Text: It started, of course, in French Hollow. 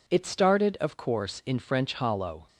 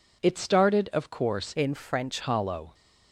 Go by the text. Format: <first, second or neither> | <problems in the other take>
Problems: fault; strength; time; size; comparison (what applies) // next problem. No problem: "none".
first | changes voice from "in" to "French"; from 1.5 to 2.1 s; 0.6 s long